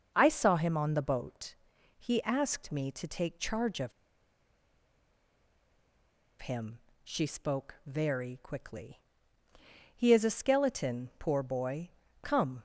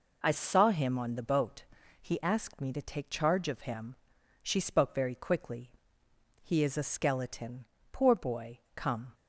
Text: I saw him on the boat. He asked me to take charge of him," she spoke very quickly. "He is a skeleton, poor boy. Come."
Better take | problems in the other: second | pauses between "of" and "him"; strong; at 3.9 s; 2.4 s long

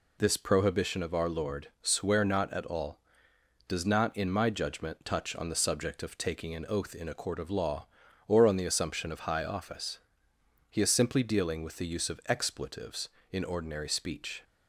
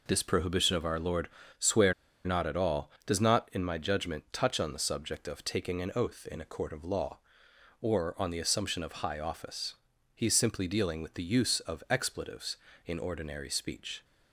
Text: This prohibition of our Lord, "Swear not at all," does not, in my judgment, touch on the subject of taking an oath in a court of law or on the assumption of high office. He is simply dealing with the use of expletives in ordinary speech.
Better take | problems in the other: first | pauses between "Swear" and "not"; slight; at 1.9 s; 0.32 s long

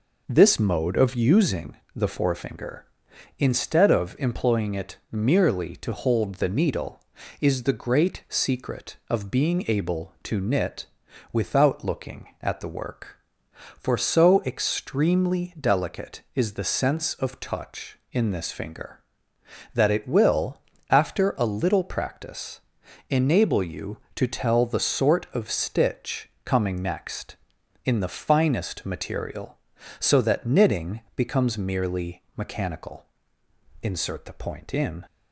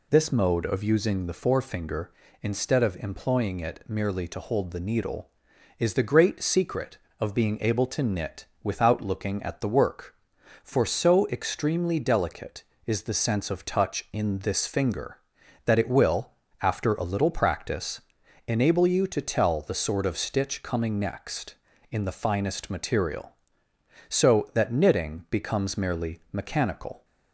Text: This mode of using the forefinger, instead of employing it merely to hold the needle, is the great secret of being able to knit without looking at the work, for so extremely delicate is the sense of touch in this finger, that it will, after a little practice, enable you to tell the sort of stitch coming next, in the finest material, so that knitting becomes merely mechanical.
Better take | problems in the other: second | pauses between "using" and "the"; slight; at 1.7 s; 0.18 s long // pauses between "it" and "merely"; slight; at 4.9 s; 0.16 s long // pauses between "knit" and "without"; noticeable; at 10.8 s; 0.48 s long; slight in the second // pauses between "stitch" and "coming"; slight; at 26.2 s; 0.16 s long // pauses between "merely" and "mechanical"; slight; at 32.2 s; 0.16 s long // goes on to say "Insert the point in"; noticeable; from 33.8 s on; 1.1 s long

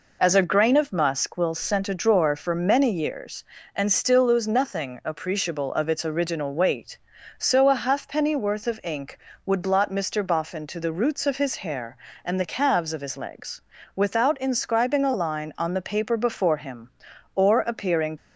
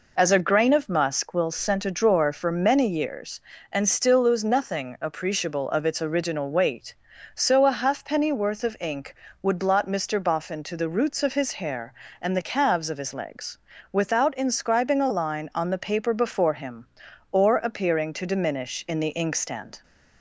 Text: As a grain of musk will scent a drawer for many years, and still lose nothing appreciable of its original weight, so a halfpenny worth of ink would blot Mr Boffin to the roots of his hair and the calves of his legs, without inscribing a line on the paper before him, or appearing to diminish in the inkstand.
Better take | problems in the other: second | stops before "to diminish in the inkstand"; at 18.1 s

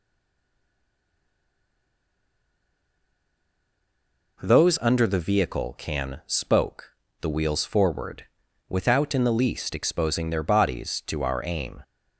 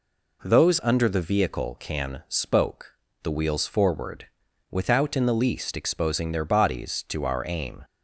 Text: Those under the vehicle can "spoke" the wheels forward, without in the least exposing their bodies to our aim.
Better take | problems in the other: second | stays silent before the first word; strong; until 4.3 s; 4.3 s long // pauses between "spoke" and "the"; slight; at 6.9 s; 0.30 s long; slight in the second

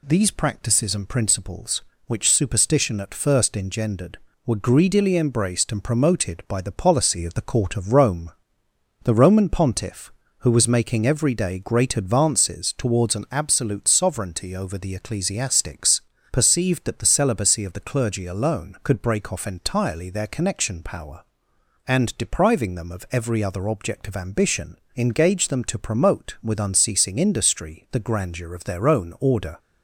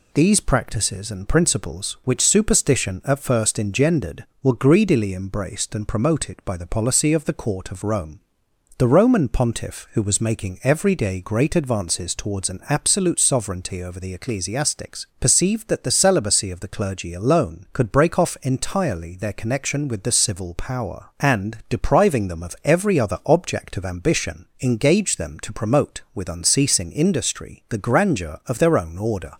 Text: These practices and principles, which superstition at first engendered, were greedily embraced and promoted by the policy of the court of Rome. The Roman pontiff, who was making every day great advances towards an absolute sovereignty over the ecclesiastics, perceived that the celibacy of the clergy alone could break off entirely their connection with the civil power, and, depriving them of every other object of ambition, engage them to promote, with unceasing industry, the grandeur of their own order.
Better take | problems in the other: second | skips "with the civil"; at 20.8 s

